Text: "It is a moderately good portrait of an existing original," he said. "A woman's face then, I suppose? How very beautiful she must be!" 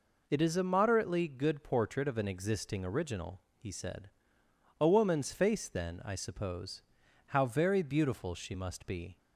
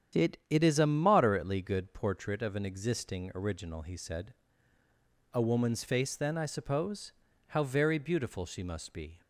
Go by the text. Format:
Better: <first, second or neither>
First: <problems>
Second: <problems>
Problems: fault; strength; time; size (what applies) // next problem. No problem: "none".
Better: first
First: none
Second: starts louder than the rest; strong; until 1.2 s; 9 dB // says "It" twice; at 0.4 s